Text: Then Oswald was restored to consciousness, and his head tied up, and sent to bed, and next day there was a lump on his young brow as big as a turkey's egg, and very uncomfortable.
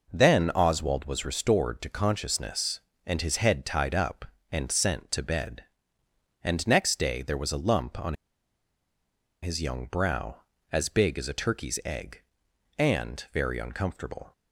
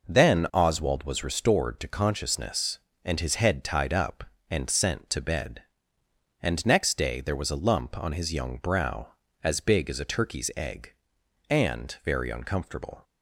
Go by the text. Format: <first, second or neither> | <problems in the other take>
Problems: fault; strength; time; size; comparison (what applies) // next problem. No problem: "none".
second | pauses between "on" and "his"; strong; at 8.1 s; 1.2 s long